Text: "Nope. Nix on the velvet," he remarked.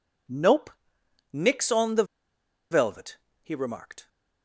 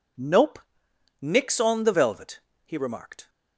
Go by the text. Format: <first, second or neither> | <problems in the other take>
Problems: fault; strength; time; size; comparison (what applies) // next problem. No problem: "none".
second | pauses between "the" and "velvet"; noticeable; at 2.0 s; 0.67 s long